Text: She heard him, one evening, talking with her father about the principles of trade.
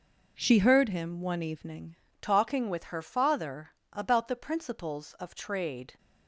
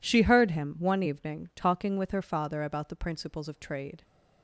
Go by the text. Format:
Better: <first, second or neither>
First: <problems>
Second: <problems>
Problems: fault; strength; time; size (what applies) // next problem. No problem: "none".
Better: second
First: changes voice at "talking"; from 2.2 s on; 3.7 s long // pauses between "father" and "about"; slight; at 3.7 s; 0.20 s long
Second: none